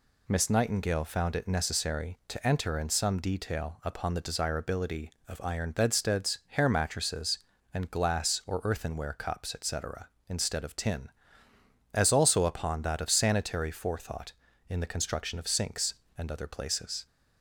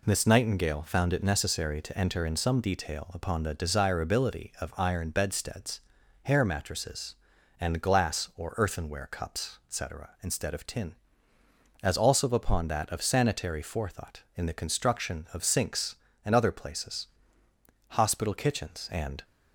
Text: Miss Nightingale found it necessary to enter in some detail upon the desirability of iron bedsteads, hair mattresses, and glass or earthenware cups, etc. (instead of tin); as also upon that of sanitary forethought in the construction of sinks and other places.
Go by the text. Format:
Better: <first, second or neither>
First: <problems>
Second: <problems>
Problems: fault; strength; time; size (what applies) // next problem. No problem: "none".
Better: first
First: none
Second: goes on to say "Hospital kitchens and"; from 17.8 s on; 1.3 s long